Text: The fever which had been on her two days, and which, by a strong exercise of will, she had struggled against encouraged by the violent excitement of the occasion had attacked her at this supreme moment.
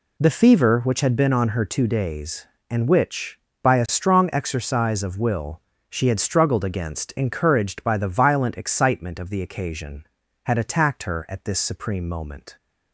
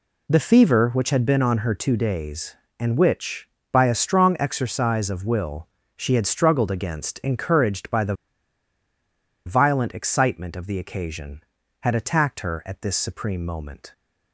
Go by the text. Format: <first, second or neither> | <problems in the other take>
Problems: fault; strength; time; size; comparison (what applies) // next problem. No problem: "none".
first | pauses between "the" and "violent"; strong; at 8.1 s; 1.3 s long